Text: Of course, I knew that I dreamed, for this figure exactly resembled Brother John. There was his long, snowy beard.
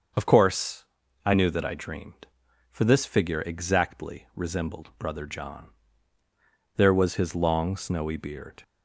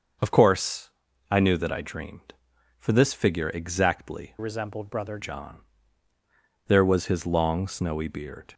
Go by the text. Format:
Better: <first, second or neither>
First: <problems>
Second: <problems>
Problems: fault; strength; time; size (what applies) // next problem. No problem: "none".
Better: first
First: starts louder than the rest; until 1.5 s; 6.5 dB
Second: starts louder than the rest; until 1.6 s; 6.5 dB // changes voice from "resembled" to "Brother"; from 4.3 to 5.1 s; 0.8 s long